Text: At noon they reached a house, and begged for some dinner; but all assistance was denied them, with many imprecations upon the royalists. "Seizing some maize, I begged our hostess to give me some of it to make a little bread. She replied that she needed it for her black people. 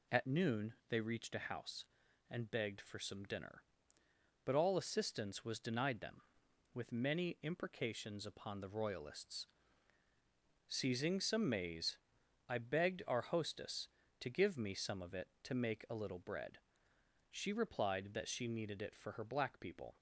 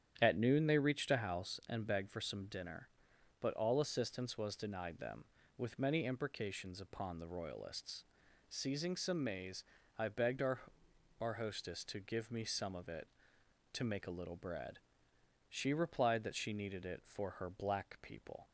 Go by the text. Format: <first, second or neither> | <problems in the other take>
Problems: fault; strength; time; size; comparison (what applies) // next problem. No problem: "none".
first | starts louder than the rest; strong; until 1.2 s; 9.5 dB // says "our" twice; at 11.2 s